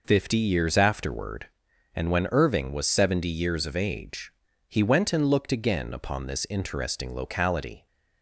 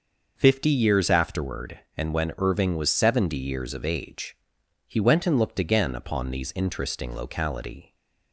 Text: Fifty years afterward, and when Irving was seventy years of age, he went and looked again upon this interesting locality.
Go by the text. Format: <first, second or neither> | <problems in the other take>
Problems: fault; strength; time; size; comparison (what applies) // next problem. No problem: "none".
first | starts louder than the rest; noticeable; until 1.3 s; 6 dB // says "these" for "this"; at 6.2 s